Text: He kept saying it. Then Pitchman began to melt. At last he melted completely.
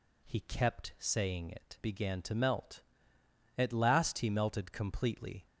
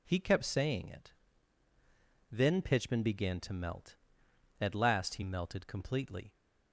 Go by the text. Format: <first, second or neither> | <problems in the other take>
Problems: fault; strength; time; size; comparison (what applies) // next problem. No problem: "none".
second | skips "Then Pitchman"; at 1.7 s